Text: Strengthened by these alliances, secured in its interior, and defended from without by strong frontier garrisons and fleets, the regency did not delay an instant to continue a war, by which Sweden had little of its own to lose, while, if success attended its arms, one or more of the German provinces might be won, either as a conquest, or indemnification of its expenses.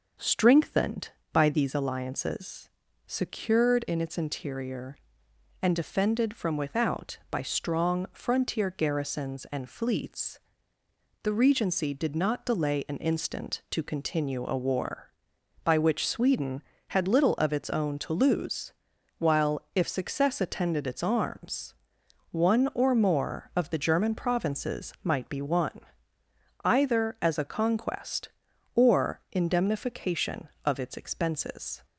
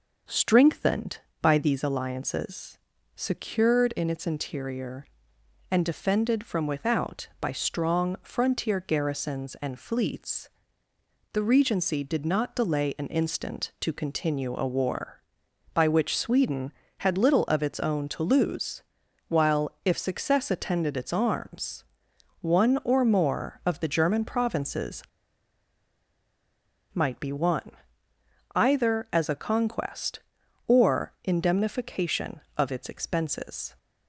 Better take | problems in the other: first | pauses between "provinces" and "might"; strong; at 25.0 s; 1.8 s long

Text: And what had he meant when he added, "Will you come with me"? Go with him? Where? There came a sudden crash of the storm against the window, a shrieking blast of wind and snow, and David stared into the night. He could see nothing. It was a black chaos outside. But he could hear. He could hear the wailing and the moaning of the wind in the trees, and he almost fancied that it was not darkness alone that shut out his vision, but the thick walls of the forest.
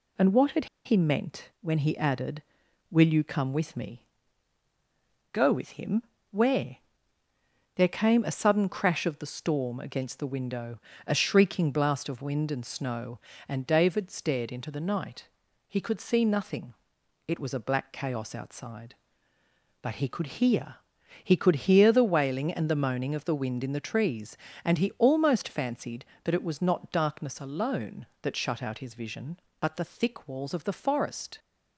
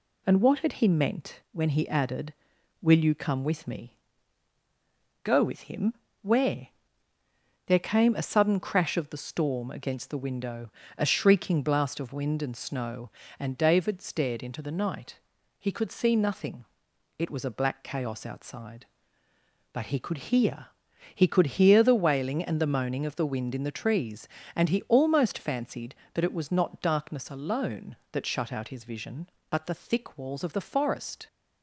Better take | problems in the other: second | pauses between "had" and "he"; slight; at 0.6 s; 0.19 s long

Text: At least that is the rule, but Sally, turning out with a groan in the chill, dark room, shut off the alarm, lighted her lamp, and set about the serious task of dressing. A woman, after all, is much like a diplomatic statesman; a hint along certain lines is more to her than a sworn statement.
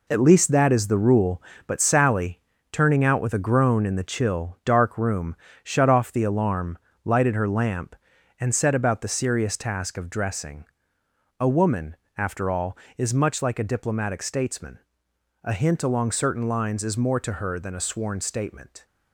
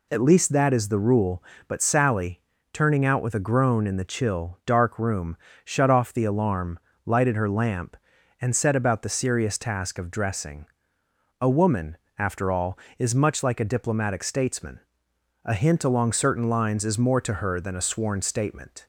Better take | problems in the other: second | gets quieter; strong; throughout; 7.5 dB

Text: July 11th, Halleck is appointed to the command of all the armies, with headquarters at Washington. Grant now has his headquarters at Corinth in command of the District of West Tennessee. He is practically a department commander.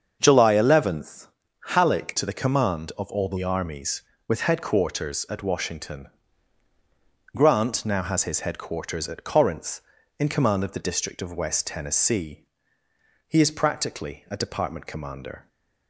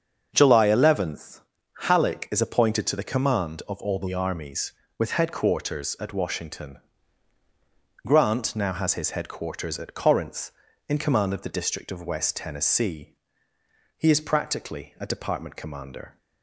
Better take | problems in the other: second | starts louder than the rest; until 1.2 s; 7 dB; also in the second // skips "is appointed"; at 2.1 s

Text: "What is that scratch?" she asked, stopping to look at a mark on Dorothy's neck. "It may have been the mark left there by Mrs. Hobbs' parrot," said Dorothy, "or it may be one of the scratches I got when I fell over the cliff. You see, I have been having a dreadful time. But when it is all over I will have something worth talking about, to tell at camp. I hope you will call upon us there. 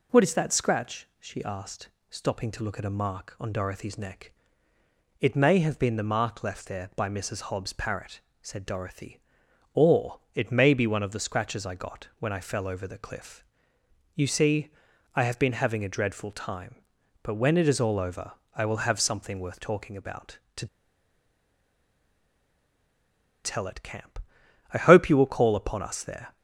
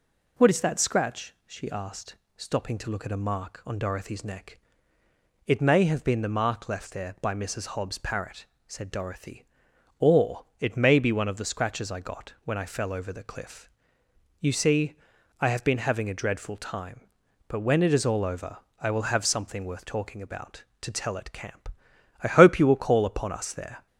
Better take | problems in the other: second | pauses between "or" and "it"; slight; at 10.1 s; 0.16 s long; slight in the second // pauses between "over" and "I"; slight; at 18.3 s; 0.20 s long; slight in the second // pauses between "to" and "tell"; strong; at 20.6 s; 2.7 s long

